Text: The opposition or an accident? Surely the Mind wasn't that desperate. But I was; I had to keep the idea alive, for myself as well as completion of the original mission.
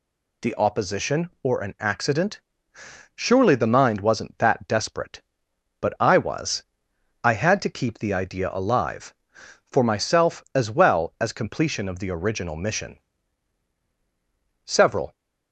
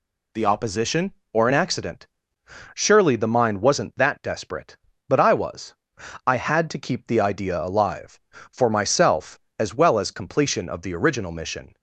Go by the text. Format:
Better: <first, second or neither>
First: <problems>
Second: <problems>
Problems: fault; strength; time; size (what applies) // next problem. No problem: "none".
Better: second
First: goes on to say "Several"; from 14.6 s on; 0.50 s long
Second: none